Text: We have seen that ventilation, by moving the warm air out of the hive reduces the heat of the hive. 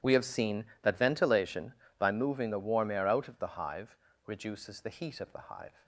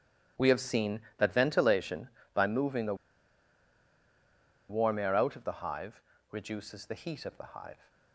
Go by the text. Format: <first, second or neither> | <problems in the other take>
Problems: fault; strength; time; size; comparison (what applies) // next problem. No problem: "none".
first | starts louder than the rest; strong; until 1.5 s; 12 dB; strong in the first // pauses between "the" and "warm"; strong; at 2.9 s; 1.7 s long // pauses between "hive" and "reduces"; slight; at 6.0 s; 0.30 s long; slight in the first